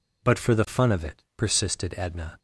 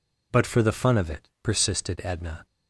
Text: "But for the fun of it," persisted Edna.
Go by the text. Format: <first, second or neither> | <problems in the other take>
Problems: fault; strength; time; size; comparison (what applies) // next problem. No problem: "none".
neither | none